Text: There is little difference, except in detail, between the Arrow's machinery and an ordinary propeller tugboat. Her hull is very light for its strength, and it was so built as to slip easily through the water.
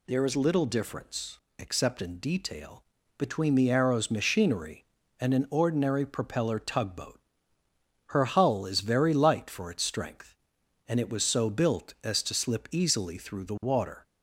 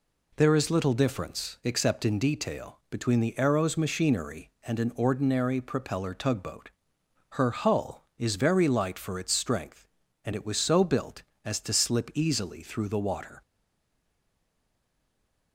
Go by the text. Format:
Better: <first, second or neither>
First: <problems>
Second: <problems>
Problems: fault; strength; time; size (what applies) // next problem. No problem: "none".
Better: first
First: none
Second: stays silent after the last word; from 13.4 s on; 2.1 s long